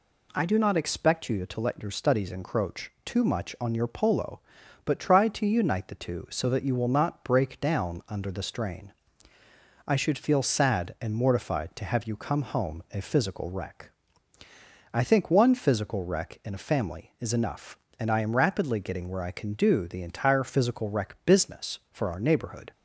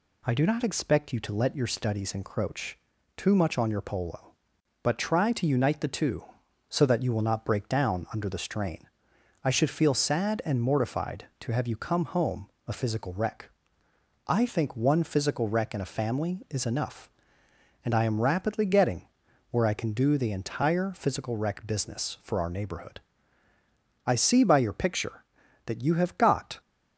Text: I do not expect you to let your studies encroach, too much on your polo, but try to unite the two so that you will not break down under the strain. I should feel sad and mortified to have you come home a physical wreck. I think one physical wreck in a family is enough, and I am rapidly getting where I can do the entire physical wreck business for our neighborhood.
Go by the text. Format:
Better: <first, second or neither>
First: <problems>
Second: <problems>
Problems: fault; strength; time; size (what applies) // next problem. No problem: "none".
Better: first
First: none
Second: pauses between "home" and "a"; slight; at 12.4 s; 0.18 s long // pauses between "getting" and "where"; at 19.0 s; 0.44 s long // goes on to say "I see by your picture that you have got"; strong; from 24.0 s on; 2.5 s long